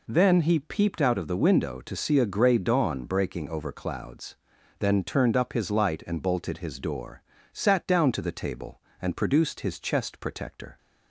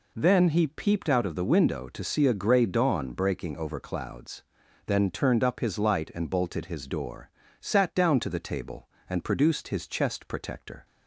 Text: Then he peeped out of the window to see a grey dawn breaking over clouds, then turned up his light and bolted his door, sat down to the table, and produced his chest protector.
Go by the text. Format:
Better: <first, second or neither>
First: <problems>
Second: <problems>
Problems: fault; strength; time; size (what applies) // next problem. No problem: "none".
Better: neither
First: none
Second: none